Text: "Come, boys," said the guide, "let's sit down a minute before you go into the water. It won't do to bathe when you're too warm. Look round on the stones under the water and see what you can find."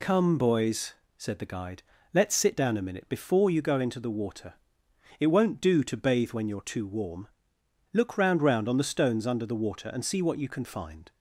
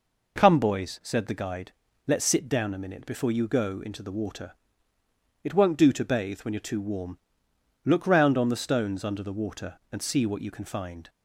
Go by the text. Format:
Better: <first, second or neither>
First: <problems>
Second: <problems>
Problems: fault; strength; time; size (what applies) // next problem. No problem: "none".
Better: second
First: says "round" twice; at 8.4 s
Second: none